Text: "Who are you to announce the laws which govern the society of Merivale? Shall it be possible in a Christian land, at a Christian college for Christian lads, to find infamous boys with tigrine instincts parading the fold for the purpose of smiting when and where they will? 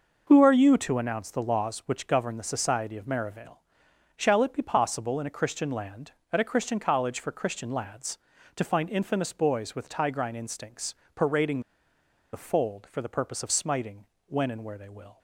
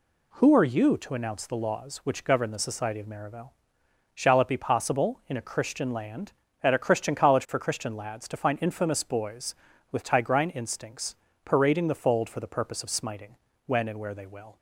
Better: second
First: pauses between "instincts" and "parading"; slight; at 10.9 s; 0.20 s long // pauses between "parading" and "the"; noticeable; at 11.5 s; 0.72 s long // pauses between "smiting" and "when"; slight; at 14.0 s; 0.20 s long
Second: pauses between "instincts" and "parading"; slight; at 11.1 s; 0.28 s long // pauses between "smiting" and "when"; slight; at 13.3 s; 0.30 s long

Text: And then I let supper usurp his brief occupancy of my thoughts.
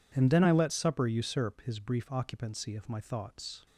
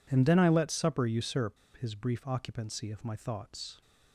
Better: first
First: none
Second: pauses between "usurp" and "his"; slight; at 1.5 s; 0.19 s long

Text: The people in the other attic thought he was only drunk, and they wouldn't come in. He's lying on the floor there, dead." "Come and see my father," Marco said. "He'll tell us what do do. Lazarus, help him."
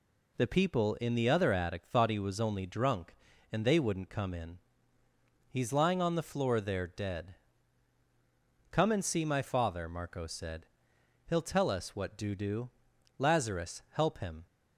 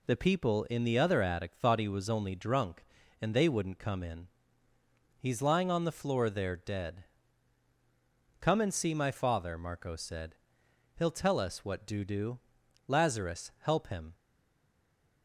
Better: first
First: none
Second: stays silent after the last word; from 14.1 s on; 1.1 s long

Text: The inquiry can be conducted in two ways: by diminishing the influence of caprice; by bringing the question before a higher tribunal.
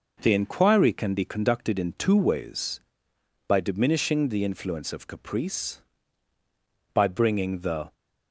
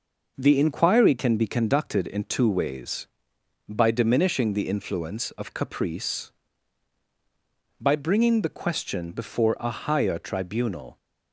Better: second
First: stops before "question before a higher tribunal"; at 7.9 s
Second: none

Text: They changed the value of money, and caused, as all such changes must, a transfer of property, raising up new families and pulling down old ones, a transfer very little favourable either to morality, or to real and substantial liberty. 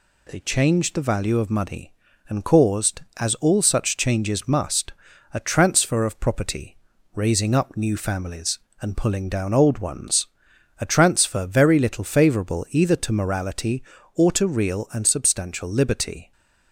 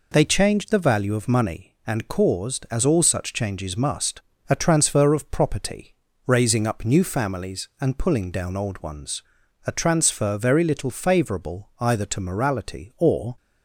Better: first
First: none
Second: stops before "to real and substantial liberty"; at 13.3 s

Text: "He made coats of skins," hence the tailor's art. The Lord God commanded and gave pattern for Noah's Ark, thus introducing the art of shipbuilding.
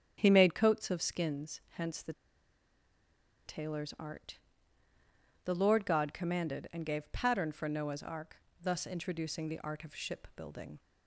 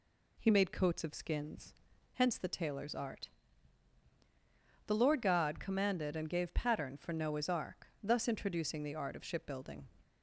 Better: second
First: starts louder than the rest; strong; until 1.1 s; 8.5 dB // pauses between "the" and "tailor's"; strong; at 2.1 s; 1.3 s long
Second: none

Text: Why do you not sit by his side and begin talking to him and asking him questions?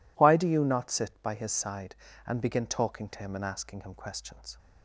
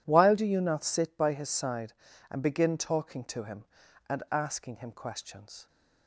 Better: first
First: none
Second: says "While" for "Why"; at 0.0 s

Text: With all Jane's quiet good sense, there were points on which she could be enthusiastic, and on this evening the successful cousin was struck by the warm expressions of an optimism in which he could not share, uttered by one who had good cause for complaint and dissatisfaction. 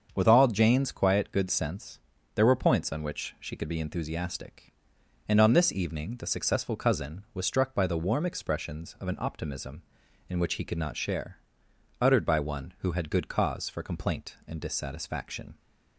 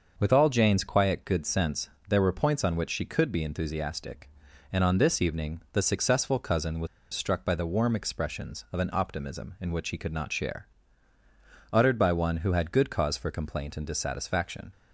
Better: first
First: starts louder than the rest; until 1.1 s; 7 dB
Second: starts louder than the rest; noticeable; until 1.1 s; 6 dB // pauses between "was" and "struck"; slight; at 6.8 s; 0.25 s long

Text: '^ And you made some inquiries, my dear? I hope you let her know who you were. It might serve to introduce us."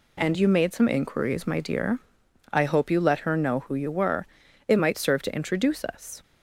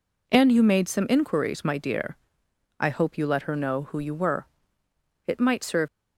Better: first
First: none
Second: stops before "to introduce us"; at 5.8 s

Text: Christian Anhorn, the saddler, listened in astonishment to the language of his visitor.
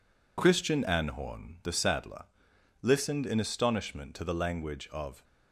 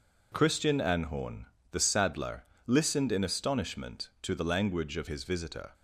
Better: second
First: stops before "his visitor"; at 5.2 s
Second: none

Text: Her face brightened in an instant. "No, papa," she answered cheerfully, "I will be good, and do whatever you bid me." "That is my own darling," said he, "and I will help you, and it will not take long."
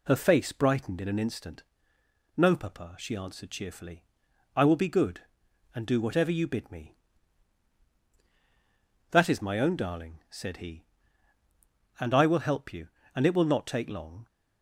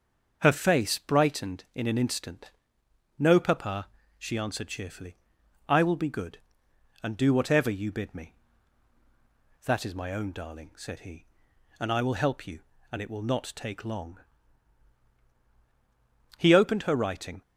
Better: first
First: none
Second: starts louder than the rest; until 1.4 s; 6.5 dB // goes on to say "He opened her writing"; noticeable; from 16.3 s on; 1.0 s long

